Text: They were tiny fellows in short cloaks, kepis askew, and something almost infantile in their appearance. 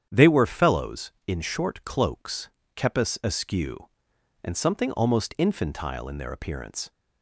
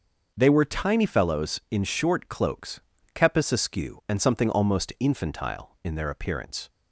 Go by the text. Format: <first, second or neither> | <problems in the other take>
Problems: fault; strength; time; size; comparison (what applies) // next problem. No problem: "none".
second | starts louder than the rest; strong; until 1.1 s; 8.5 dB; noticeable in the second // skips "tiny"; at 0.4 s